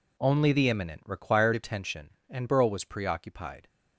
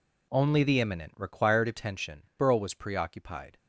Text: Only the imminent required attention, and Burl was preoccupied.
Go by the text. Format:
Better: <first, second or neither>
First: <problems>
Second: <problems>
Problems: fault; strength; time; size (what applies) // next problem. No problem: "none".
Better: first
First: none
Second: skips "and"; at 2.3 s